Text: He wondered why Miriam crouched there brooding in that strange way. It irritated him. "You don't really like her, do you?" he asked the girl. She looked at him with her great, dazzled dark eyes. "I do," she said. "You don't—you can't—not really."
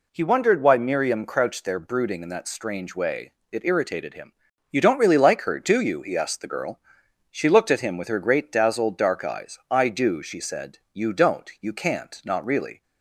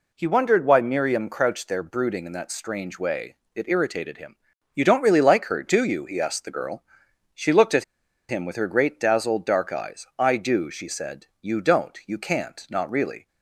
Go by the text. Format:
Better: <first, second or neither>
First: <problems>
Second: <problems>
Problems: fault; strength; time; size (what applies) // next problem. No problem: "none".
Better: first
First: none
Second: pauses between "at" and "him"; at 7.8 s; 0.44 s long